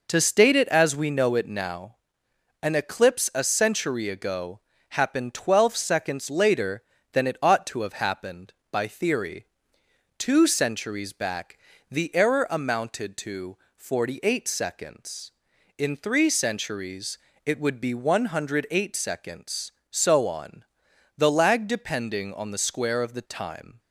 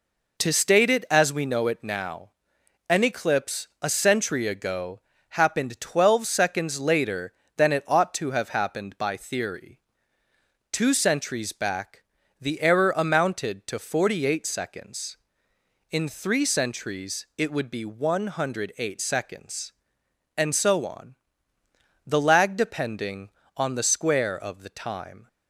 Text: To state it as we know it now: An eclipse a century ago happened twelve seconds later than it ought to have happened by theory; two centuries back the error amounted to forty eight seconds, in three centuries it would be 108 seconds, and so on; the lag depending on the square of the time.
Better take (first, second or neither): second